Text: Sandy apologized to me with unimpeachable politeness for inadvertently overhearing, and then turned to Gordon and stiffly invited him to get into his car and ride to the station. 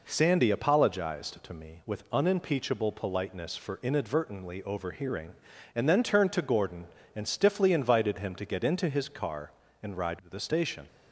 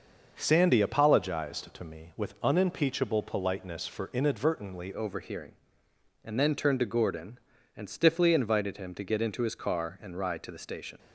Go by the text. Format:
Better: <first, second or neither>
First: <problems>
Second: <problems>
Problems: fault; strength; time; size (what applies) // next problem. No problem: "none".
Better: first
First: none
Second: starts louder than the rest; noticeable; until 1.3 s; 6 dB // changes voice at "overhearing"; from 4.9 s on; 6.0 s long